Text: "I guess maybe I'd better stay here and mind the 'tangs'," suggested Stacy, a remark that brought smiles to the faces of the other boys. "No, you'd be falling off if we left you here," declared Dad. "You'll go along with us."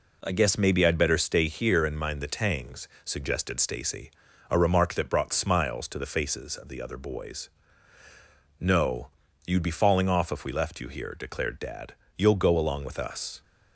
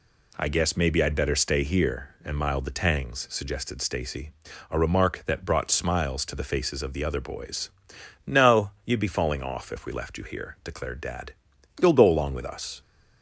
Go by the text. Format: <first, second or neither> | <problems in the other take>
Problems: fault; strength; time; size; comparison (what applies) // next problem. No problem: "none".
first | says "mild" for "mind"; at 2.3 s